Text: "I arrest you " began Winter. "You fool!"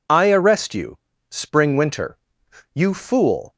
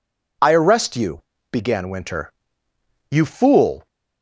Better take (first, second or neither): second